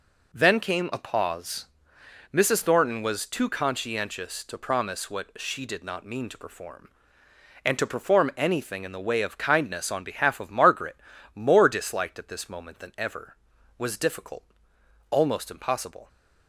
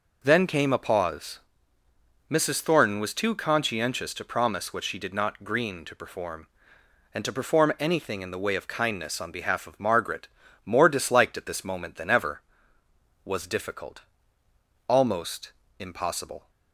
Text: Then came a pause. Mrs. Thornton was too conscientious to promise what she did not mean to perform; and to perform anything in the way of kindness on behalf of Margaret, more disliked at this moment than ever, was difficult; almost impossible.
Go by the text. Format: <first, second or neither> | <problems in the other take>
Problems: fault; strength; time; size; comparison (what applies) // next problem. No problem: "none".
first | says "green" for "mean"; at 5.4 s // pauses between "almost" and "impossible"; slight; at 15.5 s; 0.26 s long